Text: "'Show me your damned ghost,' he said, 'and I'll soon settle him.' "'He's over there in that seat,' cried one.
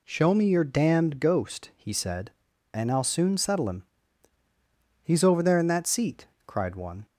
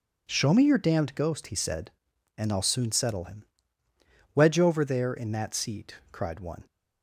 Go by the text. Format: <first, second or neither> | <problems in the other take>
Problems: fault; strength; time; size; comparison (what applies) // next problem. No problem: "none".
first | says "Wedge" for "He's"; at 4.3 s